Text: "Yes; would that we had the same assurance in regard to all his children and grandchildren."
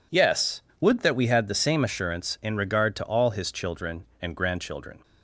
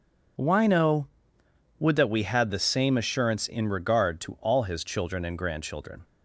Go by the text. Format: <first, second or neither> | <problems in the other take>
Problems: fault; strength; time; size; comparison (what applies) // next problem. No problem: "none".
first | says "Wino" for "Yes"; at 0.3 s